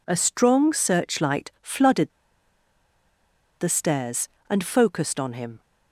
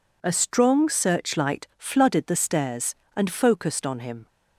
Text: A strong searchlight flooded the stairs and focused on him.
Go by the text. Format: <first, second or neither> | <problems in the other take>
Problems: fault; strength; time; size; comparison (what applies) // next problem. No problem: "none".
second | pauses between "flooded" and "the"; strong; at 2.1 s; 1.4 s long